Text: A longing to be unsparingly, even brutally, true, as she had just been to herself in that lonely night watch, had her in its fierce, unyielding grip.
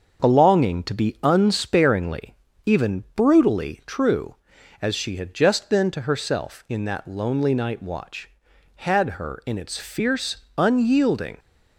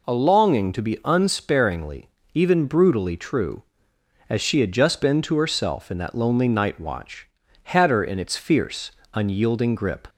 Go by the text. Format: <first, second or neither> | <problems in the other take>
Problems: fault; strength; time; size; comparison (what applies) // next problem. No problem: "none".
second | starts louder than the rest; until 1.2 s; 6.5 dB // stops before "grip"; at 11.3 s